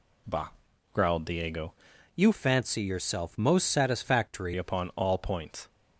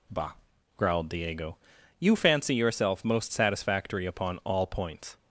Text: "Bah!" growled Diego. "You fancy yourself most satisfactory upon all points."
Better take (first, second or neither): second